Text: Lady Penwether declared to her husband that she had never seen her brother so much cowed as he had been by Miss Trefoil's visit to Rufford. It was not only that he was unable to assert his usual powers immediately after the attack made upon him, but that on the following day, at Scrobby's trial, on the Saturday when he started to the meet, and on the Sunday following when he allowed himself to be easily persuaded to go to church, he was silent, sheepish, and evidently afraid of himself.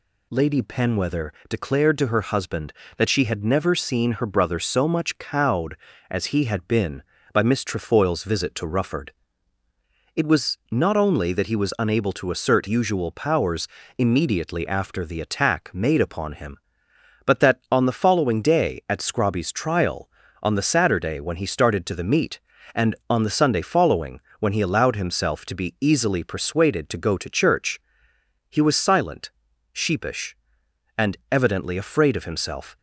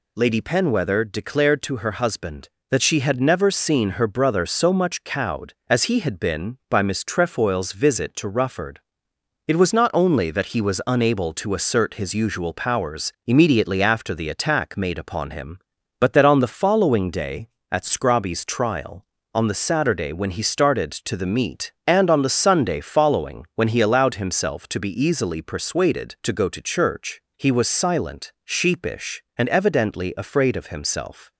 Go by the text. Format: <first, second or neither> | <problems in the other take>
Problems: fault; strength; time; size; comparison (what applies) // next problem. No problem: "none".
second | pauses between "Penwether" and "declared"; slight; at 1.3 s; 0.18 s long // skips "his"; at 12.6 s // pauses between "powers" and "immediately"; slight; at 13.6 s; 0.30 s long // pauses between "following" and "when"; slight; at 24.2 s; 0.18 s long